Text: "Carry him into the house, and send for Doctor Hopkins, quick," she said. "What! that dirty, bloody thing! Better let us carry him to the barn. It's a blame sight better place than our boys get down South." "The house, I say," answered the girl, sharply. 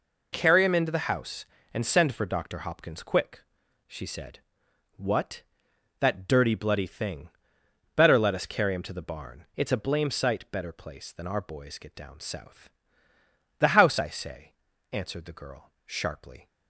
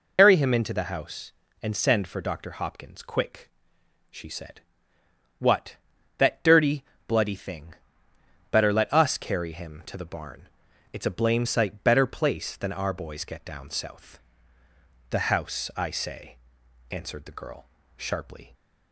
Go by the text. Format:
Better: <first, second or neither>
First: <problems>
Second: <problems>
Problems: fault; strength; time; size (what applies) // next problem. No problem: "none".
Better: first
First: none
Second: loses the start of "Carry"; at 0.1 s; 95 ms